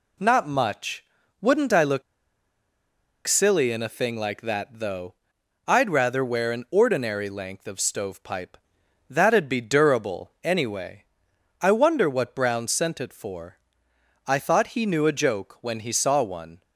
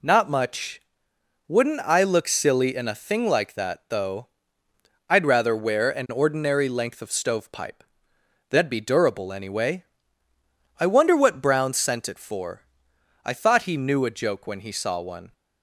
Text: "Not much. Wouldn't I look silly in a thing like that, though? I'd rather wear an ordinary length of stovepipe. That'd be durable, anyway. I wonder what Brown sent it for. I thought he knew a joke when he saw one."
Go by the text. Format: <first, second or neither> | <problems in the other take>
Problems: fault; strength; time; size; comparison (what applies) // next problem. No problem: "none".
second | pauses between "look" and "silly"; strong; at 2.0 s; 1.2 s long